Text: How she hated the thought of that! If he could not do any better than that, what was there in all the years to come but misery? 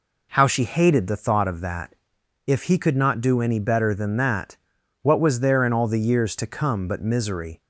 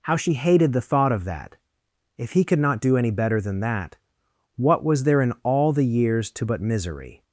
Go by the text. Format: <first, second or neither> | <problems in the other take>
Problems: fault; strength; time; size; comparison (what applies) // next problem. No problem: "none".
first | skips "come"; at 6.4 s